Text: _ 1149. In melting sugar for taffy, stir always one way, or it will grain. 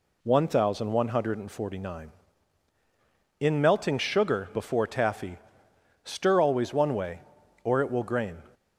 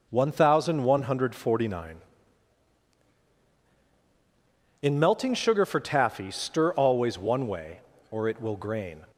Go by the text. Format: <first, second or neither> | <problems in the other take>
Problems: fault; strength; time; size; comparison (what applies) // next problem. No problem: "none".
second | says "before" for "for"; at 4.5 s